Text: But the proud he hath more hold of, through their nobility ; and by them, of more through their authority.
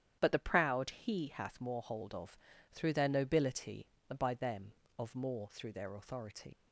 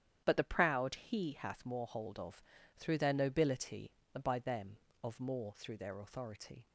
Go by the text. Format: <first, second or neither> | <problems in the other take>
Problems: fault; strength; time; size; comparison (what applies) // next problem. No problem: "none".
second | starts louder than the rest; strong; until 1.2 s; 9.5 dB; strong in the second // leaves "authority" unfinished; at 6.5 s; 110 ms